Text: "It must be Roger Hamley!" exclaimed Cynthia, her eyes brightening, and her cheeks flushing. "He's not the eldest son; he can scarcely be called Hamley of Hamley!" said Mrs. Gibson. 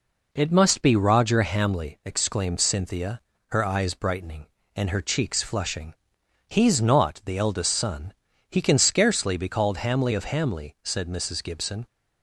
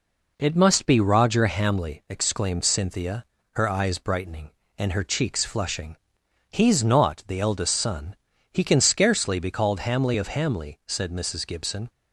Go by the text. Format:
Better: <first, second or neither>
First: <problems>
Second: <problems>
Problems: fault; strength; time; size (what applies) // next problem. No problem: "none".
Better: neither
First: none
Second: none